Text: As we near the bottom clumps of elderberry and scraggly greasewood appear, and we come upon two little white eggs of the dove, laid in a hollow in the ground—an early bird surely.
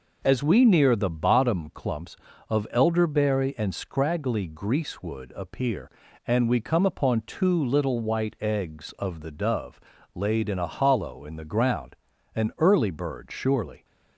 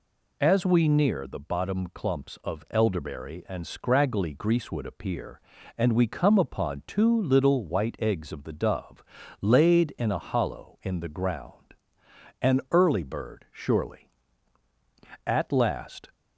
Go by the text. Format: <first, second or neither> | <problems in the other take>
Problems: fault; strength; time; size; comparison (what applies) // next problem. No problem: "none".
first | goes on to say "At last"; noticeable; from 15.2 s on; 0.84 s long